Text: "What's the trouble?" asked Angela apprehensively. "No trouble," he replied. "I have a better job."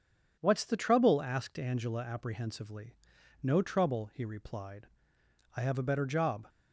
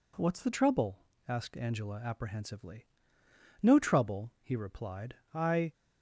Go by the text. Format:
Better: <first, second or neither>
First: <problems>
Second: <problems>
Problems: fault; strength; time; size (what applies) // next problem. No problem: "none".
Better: first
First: none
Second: stops before "have a better job"; at 5.7 s